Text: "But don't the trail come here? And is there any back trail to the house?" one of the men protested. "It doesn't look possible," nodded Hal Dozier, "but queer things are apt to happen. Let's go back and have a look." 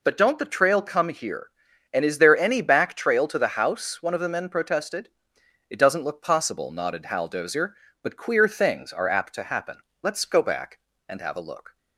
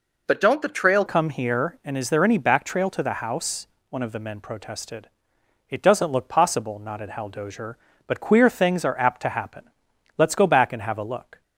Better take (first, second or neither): first